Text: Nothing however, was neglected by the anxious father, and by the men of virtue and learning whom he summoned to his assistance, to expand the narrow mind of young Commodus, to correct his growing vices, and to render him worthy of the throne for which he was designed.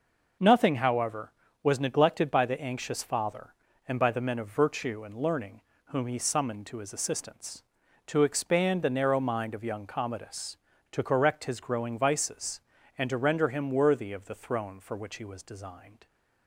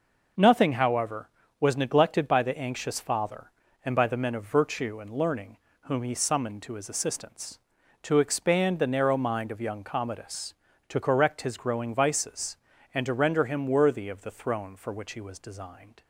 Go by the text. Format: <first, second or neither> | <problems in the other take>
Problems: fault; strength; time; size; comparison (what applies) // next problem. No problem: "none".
neither | pauses between "learning" and "whom"; slight; the same in both